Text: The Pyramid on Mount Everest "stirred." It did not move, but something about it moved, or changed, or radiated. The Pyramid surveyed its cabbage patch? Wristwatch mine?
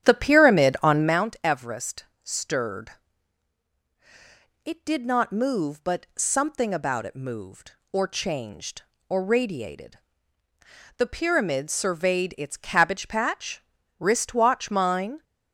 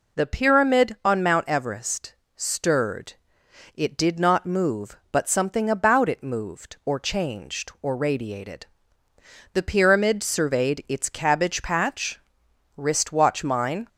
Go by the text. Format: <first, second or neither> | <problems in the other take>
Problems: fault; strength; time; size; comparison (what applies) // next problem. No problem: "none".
second | starts louder than the rest; strong; until 1.2 s; 10 dB // pauses between "Everest" and "stirred"; slight; at 2.0 s; 0.22 s long; slight in the second